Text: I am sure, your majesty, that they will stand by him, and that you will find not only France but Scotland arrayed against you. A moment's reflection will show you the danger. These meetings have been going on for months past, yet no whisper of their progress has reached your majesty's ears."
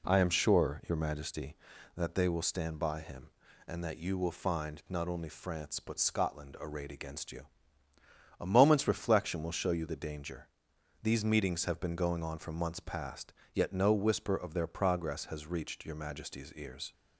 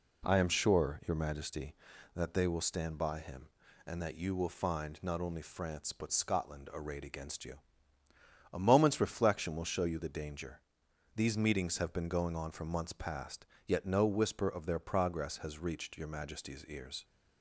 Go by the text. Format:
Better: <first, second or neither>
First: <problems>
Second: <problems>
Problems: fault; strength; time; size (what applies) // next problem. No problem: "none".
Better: neither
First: none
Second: none